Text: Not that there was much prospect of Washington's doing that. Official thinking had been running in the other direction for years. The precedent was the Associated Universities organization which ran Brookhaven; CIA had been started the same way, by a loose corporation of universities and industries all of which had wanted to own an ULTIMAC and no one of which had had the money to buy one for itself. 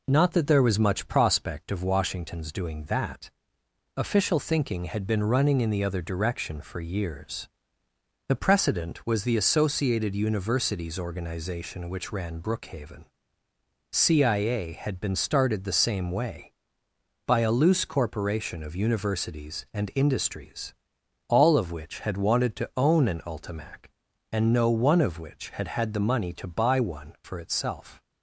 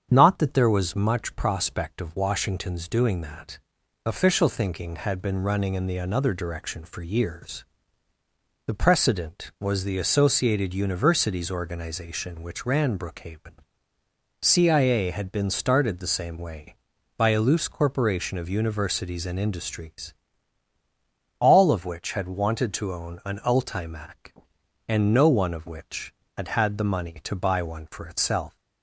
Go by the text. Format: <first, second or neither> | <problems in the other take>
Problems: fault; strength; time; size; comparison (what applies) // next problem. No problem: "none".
first | starts louder than the rest; strong; until 1.1 s; 8 dB // says "another" for "other"; at 5.9 s // pauses between "industries" and "all"; strong; at 20.1 s; 1.2 s long; noticeable in the first